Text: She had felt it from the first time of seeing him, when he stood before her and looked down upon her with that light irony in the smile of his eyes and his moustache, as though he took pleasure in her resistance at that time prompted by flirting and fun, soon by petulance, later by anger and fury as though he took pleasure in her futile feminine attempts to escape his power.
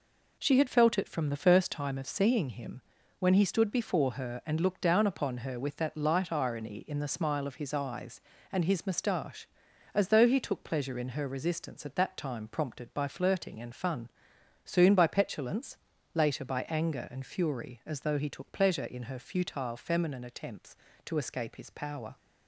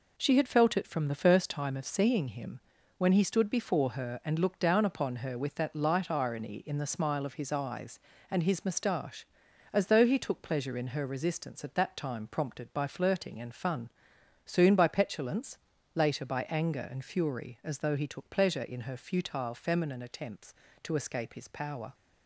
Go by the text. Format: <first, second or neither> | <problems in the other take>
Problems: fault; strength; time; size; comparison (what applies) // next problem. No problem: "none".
neither | none